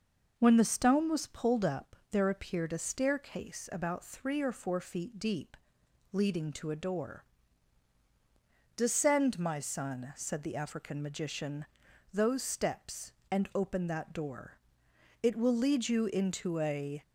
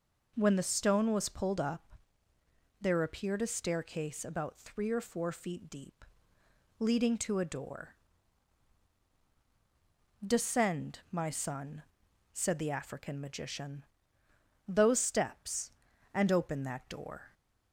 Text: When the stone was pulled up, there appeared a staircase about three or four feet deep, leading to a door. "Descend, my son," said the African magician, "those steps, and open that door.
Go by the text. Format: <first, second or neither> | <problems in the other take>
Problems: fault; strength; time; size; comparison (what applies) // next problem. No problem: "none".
second | goes on to say "It will lead you into a"; strong; from 15.2 s on; 1.8 s long